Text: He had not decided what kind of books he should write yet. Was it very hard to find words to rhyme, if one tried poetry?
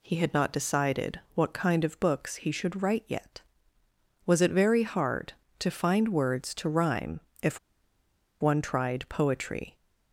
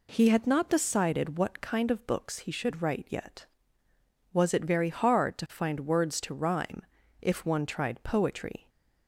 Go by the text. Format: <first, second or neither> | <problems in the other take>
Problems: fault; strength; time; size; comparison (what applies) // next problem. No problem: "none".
second | pauses between "decided" and "what"; slight; at 1.1 s; 0.16 s long // pauses between "if" and "one"; noticeable; at 7.5 s; 0.82 s long